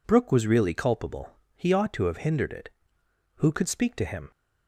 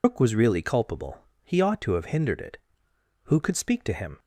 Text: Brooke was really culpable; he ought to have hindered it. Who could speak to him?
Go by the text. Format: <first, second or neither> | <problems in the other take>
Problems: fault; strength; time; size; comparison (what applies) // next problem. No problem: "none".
first | loses the start of "Brooke"; at 0.0 s; 100 ms